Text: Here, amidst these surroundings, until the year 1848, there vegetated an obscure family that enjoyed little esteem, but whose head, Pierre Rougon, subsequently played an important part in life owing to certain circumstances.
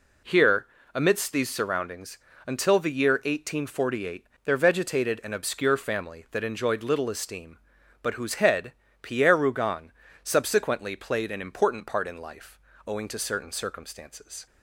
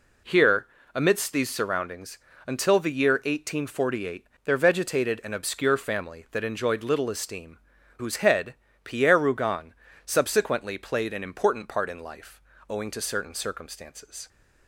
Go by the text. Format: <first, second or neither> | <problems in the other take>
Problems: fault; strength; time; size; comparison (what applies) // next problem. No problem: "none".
first | skips "but"; at 7.7 s // pauses between "life" and "owing"; slight; at 12.4 s; 0.30 s long; slight in the first